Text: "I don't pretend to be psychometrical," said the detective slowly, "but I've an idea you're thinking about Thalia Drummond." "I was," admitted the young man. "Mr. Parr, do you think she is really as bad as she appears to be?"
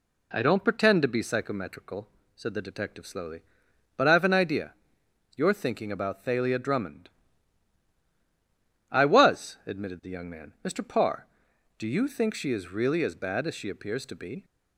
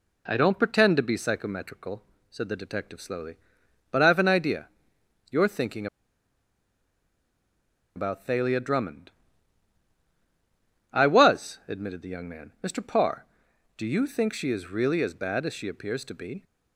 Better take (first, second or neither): first